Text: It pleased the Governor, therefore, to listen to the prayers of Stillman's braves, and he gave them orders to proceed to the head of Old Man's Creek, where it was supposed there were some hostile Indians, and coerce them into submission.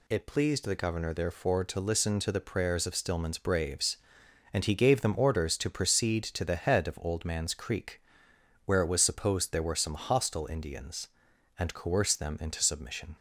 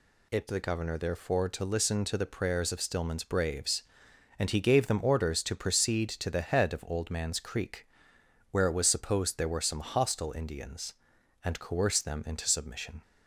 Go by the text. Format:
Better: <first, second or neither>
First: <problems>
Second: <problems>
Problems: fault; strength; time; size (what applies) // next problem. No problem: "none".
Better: first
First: none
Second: skips "pleased"; at 0.4 s